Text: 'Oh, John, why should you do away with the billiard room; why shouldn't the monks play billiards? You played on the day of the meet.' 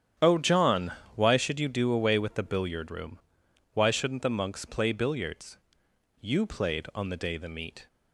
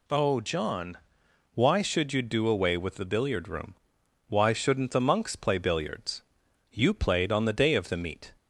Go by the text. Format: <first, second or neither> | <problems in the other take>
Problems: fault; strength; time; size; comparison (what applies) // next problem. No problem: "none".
second | starts louder than the rest; strong; until 1.4 s; 9.5 dB // skips "of"; at 7.3 s